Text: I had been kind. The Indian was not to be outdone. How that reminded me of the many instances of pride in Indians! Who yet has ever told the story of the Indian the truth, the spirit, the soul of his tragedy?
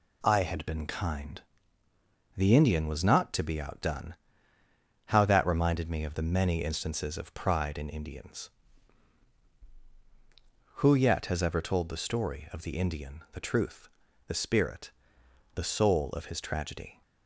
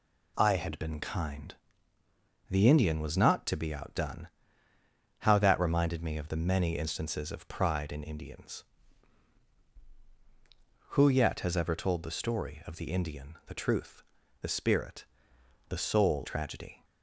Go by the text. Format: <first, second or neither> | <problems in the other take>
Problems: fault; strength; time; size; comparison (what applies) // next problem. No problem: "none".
first | skips "of his"; at 16.2 s